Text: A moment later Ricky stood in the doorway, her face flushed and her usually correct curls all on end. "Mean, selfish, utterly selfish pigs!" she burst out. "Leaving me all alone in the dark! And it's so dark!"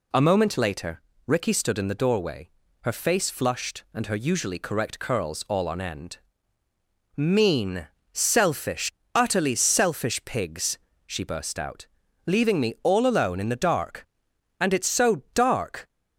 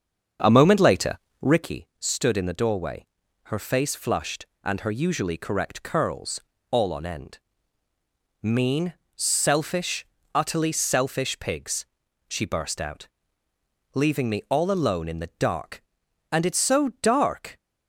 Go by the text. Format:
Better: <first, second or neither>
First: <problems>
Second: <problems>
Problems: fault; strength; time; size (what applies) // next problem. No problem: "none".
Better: first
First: pauses between "later" and "Ricky"; slight; at 1.0 s; 0.26 s long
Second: starts louder than the rest; until 1.8 s; 7 dB // pauses between "later" and "Ricky"; slight; at 1.1 s; 0.24 s long // pauses between "curls" and "all"; slight; at 6.4 s; 0.30 s long